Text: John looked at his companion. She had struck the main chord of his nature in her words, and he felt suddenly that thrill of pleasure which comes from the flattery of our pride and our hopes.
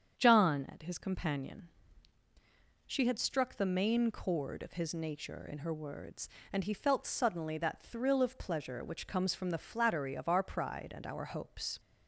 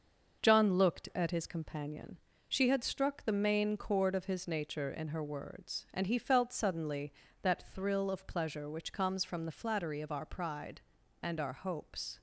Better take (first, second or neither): second